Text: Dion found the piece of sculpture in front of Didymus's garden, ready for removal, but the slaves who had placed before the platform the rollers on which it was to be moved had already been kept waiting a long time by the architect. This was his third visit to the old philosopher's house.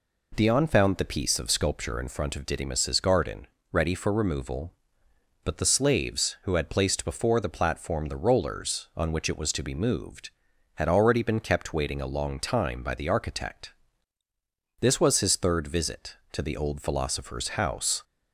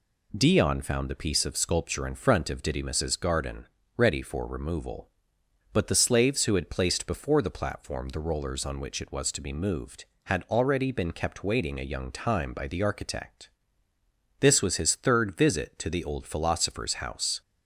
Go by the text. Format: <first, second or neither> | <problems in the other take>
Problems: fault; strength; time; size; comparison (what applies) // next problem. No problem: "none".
first | says "young" for "long"; at 11.9 s